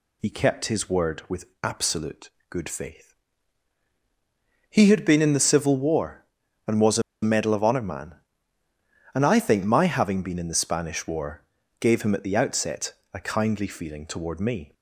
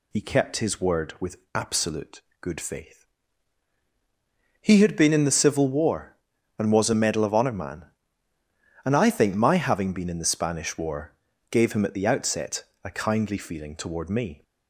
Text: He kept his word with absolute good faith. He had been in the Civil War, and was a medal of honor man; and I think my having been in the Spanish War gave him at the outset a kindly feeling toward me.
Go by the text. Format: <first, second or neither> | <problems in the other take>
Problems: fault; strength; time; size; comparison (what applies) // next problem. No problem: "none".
second | pauses between "with" and "absolute"; slight; at 1.4 s; 0.16 s long; slight in the second // pauses between "absolute" and "good"; slight; at 2.2 s; 0.22 s long; slight in the second // pauses between "a" and "medal"; slight; at 7.0 s; 0.20 s long // pauses between "War" and "gave"; slight; at 11.4 s; 0.36 s long; slight in the second // pauses between "outset" and "a"; slight; at 12.9 s; 0.20 s long; slight in the second